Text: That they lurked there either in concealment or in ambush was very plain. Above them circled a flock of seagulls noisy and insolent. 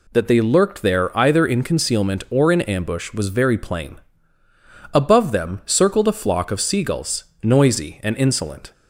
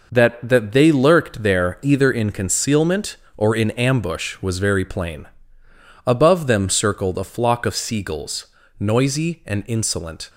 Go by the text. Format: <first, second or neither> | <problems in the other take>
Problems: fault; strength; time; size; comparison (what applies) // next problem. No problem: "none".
first | says "That" twice; at 0.4 s // pauses between "seagulls" and "noisy"; slight; at 8.4 s; 0.32 s long; slight in the first